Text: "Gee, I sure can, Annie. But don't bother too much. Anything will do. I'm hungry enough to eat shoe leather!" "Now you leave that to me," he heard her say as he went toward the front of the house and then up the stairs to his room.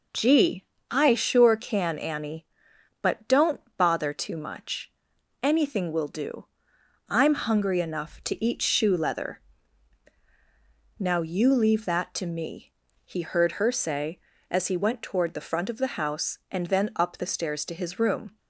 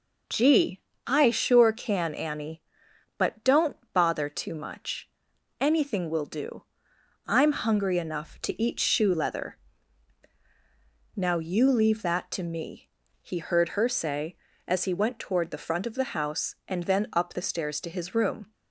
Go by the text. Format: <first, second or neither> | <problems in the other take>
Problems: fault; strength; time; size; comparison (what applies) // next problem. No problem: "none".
neither | pauses between "don't" and "bother"; slight; the same in both